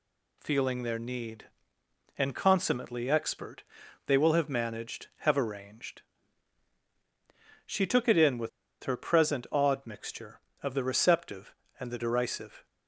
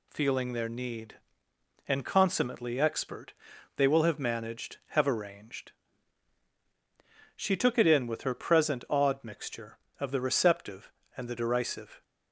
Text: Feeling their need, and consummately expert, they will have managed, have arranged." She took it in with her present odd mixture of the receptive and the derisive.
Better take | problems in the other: second | pauses between "with" and "her"; slight; at 8.4 s; 0.33 s long

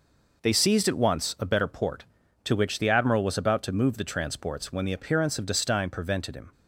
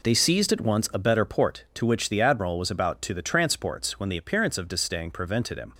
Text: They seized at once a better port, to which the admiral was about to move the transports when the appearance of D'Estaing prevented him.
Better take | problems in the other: first | skips "move"; at 3.1 s

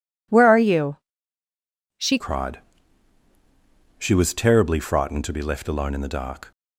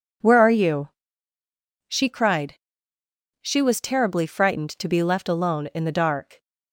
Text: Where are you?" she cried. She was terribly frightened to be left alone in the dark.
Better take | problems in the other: second | changes voice at "cried"; from 2.1 s on; 4.4 s long

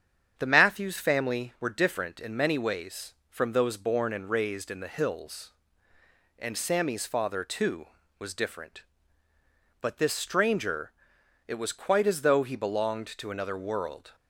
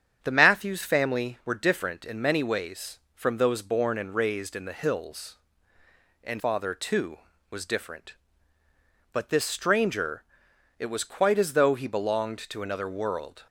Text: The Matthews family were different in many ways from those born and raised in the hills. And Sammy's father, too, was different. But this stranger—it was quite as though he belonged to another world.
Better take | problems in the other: first | starts louder than the rest; strong; until 1.2 s; 8.5 dB; strong in the first // skips "Sammy's"; at 6.3 s

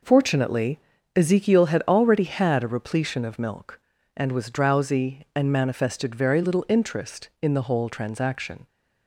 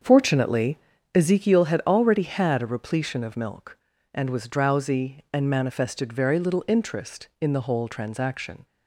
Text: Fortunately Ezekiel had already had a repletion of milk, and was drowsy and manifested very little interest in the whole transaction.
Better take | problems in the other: first | starts louder than the rest; until 1.4 s; 7 dB // pauses between "Fortunately" and "Ezekiel"; slight; at 0.7 s; 0.36 s long; slight in the first

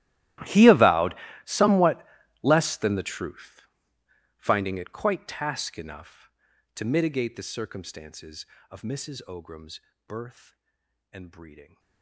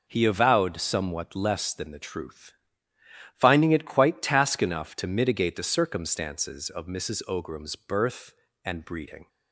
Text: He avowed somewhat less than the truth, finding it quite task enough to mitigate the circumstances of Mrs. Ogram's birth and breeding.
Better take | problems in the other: second | gets quieter; strong; throughout; 23 dB // pauses between "avowed" and "somewhat"; slight; at 1.1 s; 0.30 s long // pauses between "somewhat" and "less"; slight; at 2.0 s; 0.36 s long // pauses between "Ogram's" and "birth"; slight; at 9.8 s; 0.26 s long

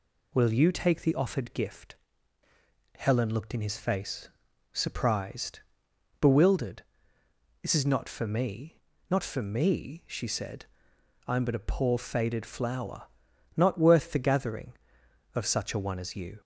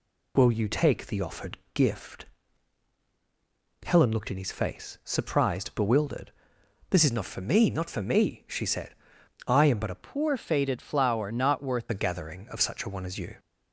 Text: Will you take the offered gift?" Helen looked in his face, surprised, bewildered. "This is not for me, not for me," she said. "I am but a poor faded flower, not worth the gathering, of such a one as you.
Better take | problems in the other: first | pauses between "offered" and "gift"; slight; at 1.5 s; 0.16 s long // changes voice from "poor" to "worth"; from 10.0 to 11.8 s; 1.8 s long

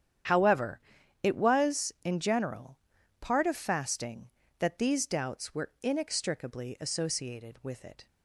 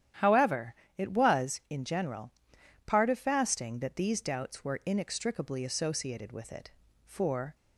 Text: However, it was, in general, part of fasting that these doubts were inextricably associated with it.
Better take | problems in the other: first | starts louder than the rest; strong; until 1.4 s; 10.5 dB; strong in the first // goes on to say "For"; from 7.0 s on; 0.50 s long

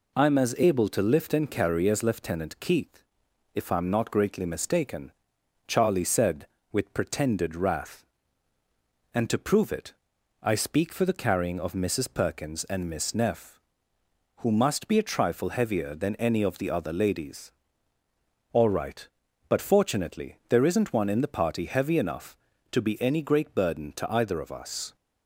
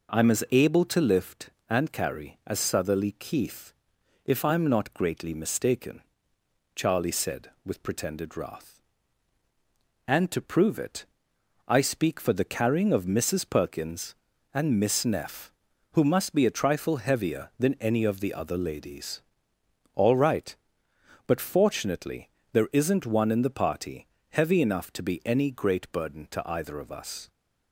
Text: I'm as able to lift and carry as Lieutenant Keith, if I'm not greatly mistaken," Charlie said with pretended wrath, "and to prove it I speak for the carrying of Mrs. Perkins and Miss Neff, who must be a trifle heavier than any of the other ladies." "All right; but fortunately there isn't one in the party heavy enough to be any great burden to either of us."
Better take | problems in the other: first | says "Southerly" for "Lieutenant"; at 2.5 s // pauses between "it" and "I"; noticeable; at 11.0 s; 0.62 s long; noticeable in the first // pauses between "fortunately" and "there"; slight; at 22.3 s; 0.22 s long // pauses between "party" and "heavy"; slight; at 24.0 s; 0.22 s long

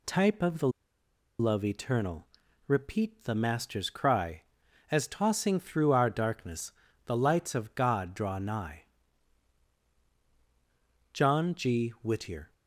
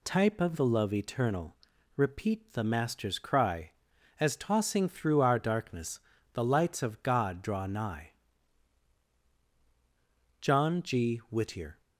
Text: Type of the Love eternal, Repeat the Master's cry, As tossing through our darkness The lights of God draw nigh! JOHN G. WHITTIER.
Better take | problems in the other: second | pauses between "the" and "Love"; noticeable; at 0.6 s; 0.70 s long // pauses between "darkness" and "The"; slight; at 6.7 s; 0.34 s long; slight in the second

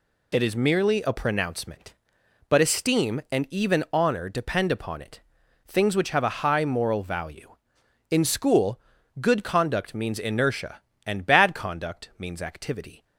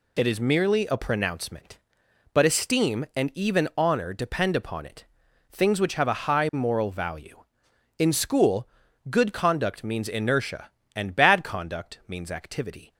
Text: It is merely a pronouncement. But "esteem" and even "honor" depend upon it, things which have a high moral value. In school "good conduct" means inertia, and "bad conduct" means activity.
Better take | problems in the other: neither | pauses between "school" and "good"; the same in both

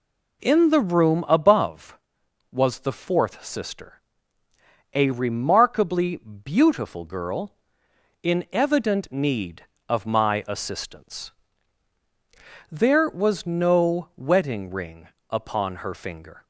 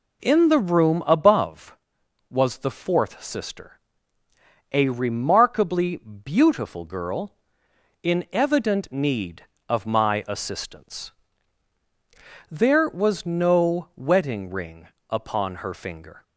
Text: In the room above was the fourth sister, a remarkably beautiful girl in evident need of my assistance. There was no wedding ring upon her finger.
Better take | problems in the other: neither | pauses between "ring" and "upon"; slight; the same in both

